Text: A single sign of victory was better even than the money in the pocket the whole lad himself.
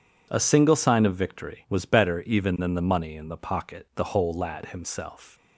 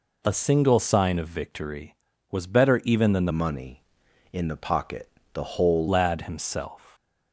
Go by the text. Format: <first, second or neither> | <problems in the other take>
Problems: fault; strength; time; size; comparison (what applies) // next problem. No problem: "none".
first | changes voice from "money" to "whole"; from 3.2 to 5.8 s; 2.6 s long // pauses between "pocket" and "the"; slight; at 5.0 s; 0.26 s long